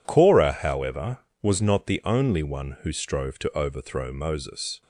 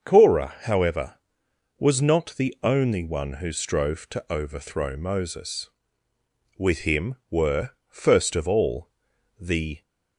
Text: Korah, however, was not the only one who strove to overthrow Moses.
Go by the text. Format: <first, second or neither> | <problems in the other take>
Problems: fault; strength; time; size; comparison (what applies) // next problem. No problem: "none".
first | starts louder than the rest; until 1.1 s; 6.5 dB // goes on to say "With him were first of all the"; strong; from 6.5 s on; 3.2 s long